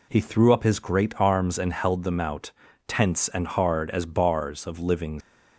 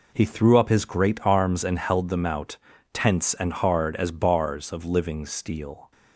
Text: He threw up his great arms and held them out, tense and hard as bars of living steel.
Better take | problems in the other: second | stops before "steel"; at 5.2 s

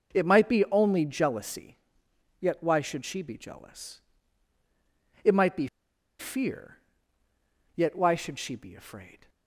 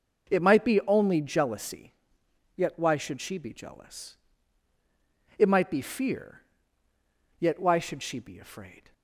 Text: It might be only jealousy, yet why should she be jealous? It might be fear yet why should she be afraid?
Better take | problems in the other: second | pauses between "be" and "fear"; noticeable; at 5.6 s; 0.52 s long // pauses between "fear" and "yet"; at 6.7 s; 1.0 s long; also in the second

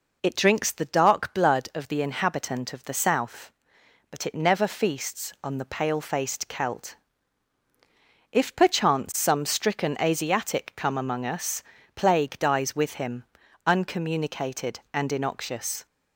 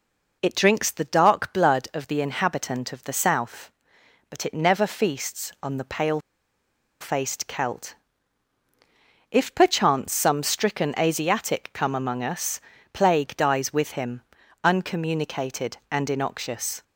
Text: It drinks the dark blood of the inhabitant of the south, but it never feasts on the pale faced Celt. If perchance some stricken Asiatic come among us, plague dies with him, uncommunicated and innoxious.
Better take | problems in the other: first | pauses between "pale" and "faced"; noticeable; at 6.1 s; 0.81 s long

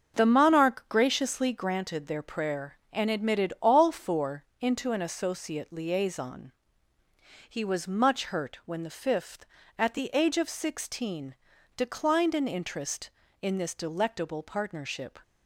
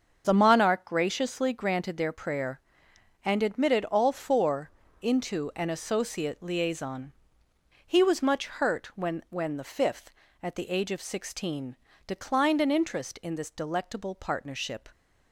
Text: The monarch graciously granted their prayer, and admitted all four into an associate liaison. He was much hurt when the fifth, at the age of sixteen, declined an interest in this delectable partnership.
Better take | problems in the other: first | starts louder than the rest; until 1.2 s; 6.5 dB; also in the first // pauses between "four" and "into"; slight; at 4.7 s; 0.28 s long; slight in the first // says "when" twice; at 9.2 s

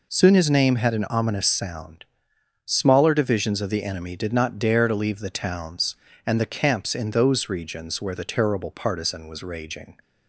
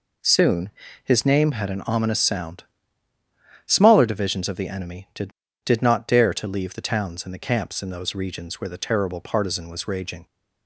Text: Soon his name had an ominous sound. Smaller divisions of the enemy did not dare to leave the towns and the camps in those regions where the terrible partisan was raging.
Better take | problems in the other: first | pauses between "Soon" and "his"; slight; at 0.6 s; 0.34 s long // says "did" twice; at 5.6 s

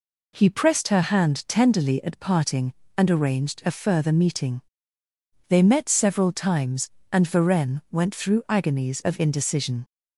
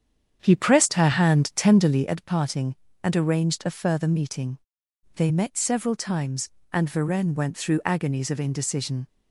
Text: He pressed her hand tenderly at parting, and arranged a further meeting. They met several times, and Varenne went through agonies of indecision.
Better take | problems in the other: first | starts louder than the rest; strong; until 2.2 s; 8 dB

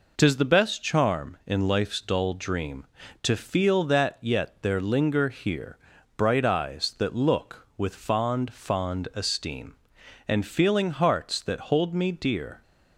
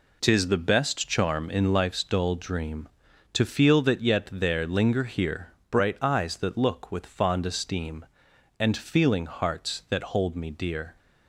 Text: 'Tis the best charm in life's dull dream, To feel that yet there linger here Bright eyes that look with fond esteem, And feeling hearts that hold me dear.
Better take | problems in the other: second | pauses between "here" and "Bright"; at 5.7 s; 0.40 s long; slight in the second // says "fond" twice; at 8.5 s

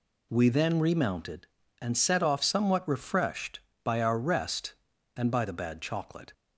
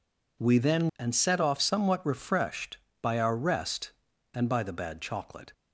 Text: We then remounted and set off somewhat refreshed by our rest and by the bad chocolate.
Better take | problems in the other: first | skips "remounted"; at 0.9 s

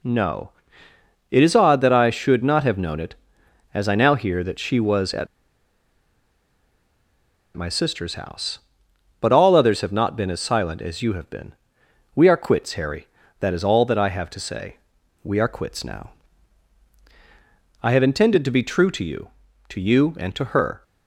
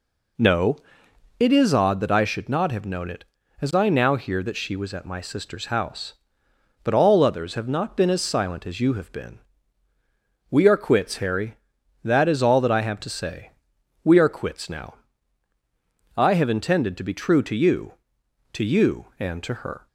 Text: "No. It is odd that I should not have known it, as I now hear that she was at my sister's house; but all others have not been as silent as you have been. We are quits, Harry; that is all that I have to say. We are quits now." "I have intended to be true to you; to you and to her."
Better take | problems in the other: second | pauses between "at" and "my"; strong; at 5.2 s; 2.2 s long

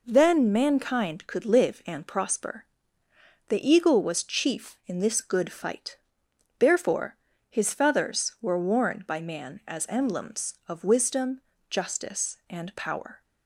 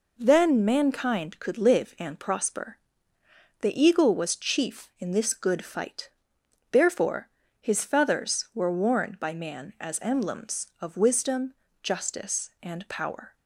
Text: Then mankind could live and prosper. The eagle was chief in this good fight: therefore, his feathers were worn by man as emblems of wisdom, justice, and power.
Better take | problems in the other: neither | none

